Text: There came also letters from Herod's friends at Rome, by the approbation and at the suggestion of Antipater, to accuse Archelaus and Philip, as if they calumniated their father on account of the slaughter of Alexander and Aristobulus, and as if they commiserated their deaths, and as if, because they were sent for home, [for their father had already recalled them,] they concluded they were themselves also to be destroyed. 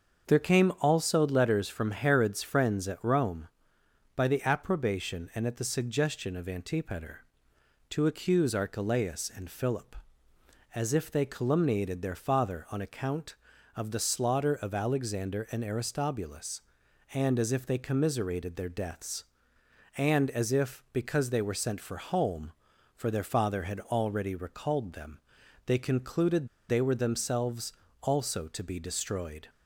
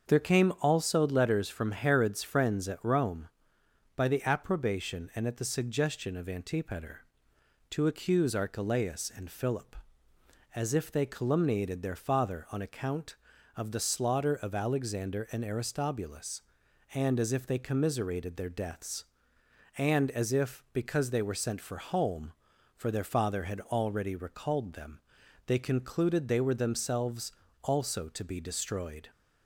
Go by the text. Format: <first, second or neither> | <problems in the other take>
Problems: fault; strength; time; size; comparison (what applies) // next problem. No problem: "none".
second | starts louder than the rest; until 1.3 s; 6.5 dB; also in the second // pauses between "concluded" and "they"; slight; at 26.4 s; 0.21 s long // pauses between "themselves" and "also"; slight; at 27.7 s; 0.28 s long; slight in the second